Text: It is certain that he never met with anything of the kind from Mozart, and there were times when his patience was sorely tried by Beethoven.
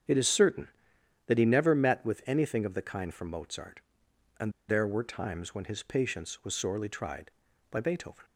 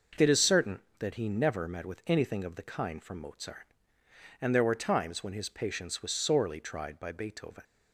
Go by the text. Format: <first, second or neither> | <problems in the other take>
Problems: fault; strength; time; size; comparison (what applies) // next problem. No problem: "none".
second | starts louder than the rest; strong; until 1.6 s; 8 dB // pauses between "and" and "there"; slight; at 4.5 s; 0.16 s long